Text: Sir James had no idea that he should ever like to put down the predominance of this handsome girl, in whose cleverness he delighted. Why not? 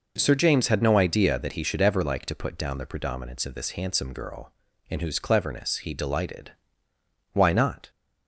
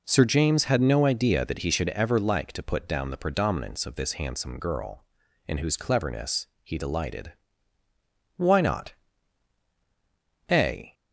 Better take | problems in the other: first | pauses between "cleverness" and "he"; slight; at 6.4 s; 0.16 s long // goes on to say "A"; slight; from 10.5 s on; 0.42 s long

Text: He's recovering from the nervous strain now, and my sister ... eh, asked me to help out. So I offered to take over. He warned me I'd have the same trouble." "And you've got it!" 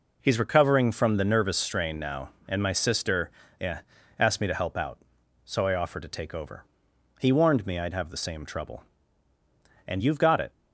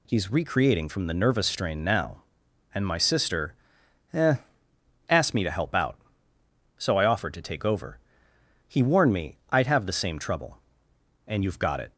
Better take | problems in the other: first | says "recreating" for "recovering"; at 0.3 s

